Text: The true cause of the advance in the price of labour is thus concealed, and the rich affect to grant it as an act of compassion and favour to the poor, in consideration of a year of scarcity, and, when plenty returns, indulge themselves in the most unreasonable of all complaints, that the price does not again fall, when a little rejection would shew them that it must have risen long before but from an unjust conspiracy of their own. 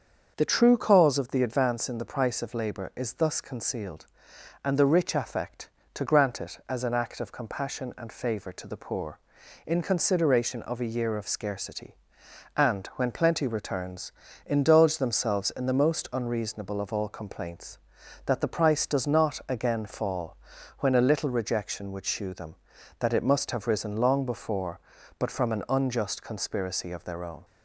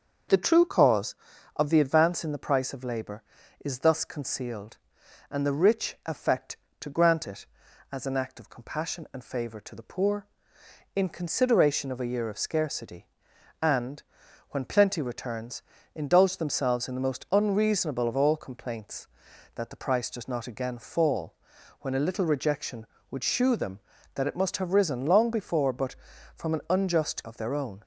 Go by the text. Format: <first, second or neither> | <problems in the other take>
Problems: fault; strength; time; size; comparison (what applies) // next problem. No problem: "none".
first | starts louder than the rest; until 1.7 s; 6.5 dB; also in the first // skips "conspiracy"; at 27.2 s